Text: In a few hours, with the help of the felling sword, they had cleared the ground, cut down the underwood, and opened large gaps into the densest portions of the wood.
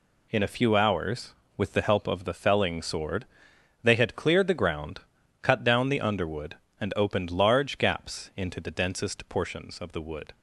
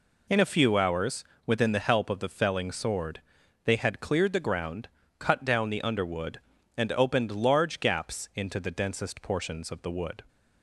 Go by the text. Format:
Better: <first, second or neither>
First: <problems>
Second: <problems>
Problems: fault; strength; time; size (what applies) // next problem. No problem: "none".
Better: first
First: none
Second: says "within" for "with"; at 1.4 s